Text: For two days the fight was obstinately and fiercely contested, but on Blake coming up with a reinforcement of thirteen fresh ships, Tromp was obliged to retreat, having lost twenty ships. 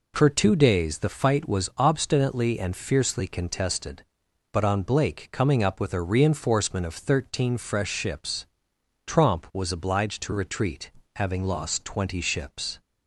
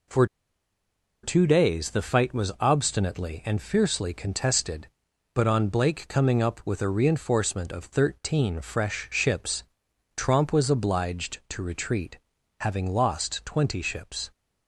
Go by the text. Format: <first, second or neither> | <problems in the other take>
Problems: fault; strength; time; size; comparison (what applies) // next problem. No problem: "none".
first | pauses between "For" and "two"; at 0.2 s; 0.98 s long